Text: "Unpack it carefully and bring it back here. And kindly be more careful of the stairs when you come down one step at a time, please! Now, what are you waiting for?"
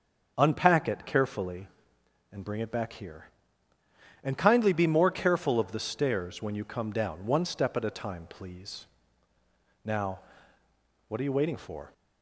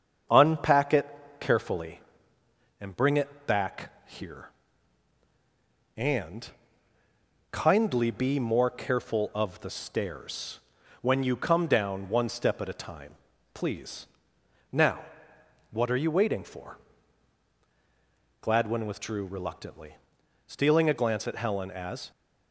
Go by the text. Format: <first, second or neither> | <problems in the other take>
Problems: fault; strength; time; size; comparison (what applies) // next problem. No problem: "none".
first | starts louder than the rest; strong; until 1.6 s; 7 dB; also in the first // pauses between "it" and "carefully"; slight; at 1.0 s; 0.32 s long // pauses between "And" and "kindly"; at 6.4 s; 1.0 s long // pauses between "stairs" and "when"; at 10.5 s; 0.42 s long // goes on to say "Gladwin withdrew reluctantly stealing a glance at Helen as"; strong; from 18.4 s on; 3.7 s long